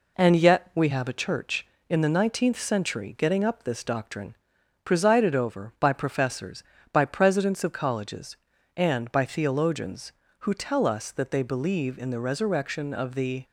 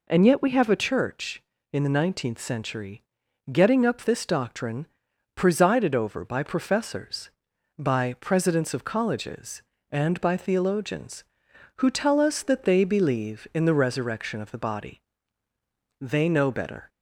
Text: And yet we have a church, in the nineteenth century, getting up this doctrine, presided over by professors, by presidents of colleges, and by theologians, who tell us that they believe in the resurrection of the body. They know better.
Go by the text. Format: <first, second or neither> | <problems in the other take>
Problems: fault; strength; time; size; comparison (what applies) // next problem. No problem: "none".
second | stops before "body They know better"; at 13.4 s